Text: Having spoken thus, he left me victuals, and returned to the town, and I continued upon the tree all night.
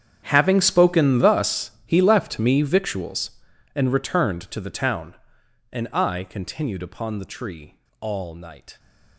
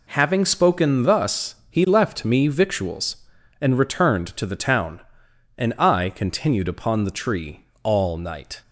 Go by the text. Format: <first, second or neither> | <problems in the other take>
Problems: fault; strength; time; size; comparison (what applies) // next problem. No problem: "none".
second | gets quieter; strong; throughout; 18 dB // pauses between "tree" and "all"; slight; at 7.7 s; 0.20 s long; slight in the second